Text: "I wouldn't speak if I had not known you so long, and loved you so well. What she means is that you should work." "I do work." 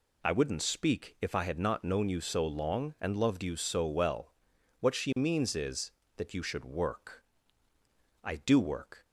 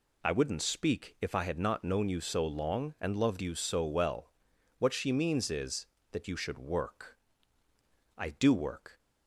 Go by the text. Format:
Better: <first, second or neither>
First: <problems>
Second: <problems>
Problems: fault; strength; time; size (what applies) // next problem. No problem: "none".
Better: neither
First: none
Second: none